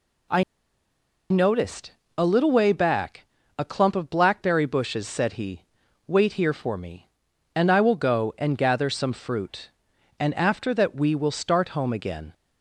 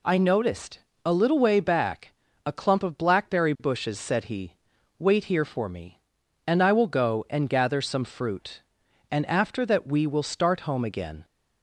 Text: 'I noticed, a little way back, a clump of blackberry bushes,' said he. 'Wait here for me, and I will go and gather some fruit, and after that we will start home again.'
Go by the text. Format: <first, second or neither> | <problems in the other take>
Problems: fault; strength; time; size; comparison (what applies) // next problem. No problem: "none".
second | pauses between "I" and "noticed"; noticeable; at 0.4 s; 0.87 s long